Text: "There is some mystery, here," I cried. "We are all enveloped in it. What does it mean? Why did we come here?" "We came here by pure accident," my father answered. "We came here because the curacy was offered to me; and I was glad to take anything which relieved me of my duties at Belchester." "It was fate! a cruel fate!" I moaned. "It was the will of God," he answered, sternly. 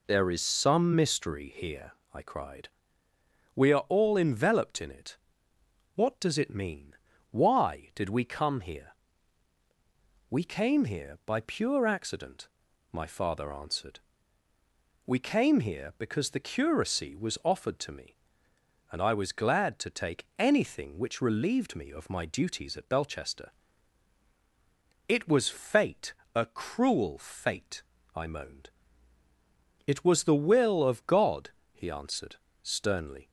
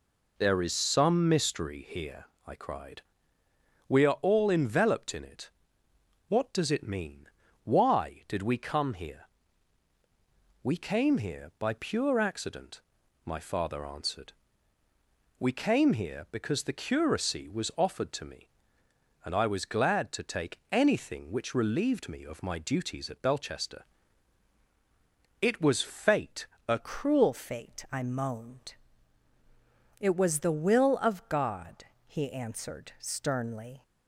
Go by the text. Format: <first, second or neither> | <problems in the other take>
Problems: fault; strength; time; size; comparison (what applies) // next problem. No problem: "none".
first | changes voice at "cruel"; from 26.7 s on; 7.1 s long